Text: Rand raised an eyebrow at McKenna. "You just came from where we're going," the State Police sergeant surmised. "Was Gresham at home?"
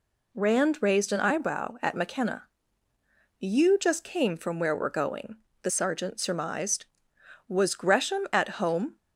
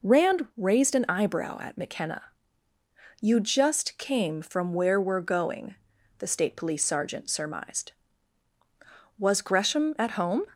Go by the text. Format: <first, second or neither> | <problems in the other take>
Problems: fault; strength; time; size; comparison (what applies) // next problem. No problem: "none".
second | skips "State Police"; at 5.7 s